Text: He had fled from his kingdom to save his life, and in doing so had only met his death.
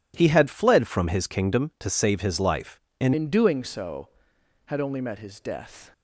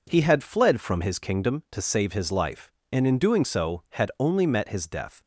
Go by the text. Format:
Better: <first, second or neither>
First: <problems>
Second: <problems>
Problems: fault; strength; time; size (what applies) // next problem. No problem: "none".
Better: second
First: changes voice at "in"; from 3.1 s on; 2.8 s long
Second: none